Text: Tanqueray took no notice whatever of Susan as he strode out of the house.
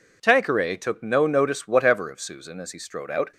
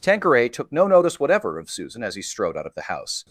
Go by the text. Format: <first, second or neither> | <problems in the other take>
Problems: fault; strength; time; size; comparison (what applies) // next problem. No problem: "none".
second | stops before "of the house"; at 3.3 s